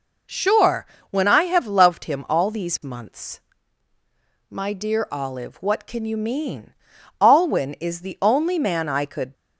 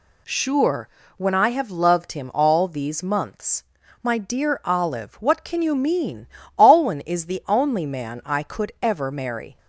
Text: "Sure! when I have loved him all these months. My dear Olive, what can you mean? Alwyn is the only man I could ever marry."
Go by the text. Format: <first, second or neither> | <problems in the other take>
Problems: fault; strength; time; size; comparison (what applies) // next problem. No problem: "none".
second | stops before "ever marry"; at 9.3 s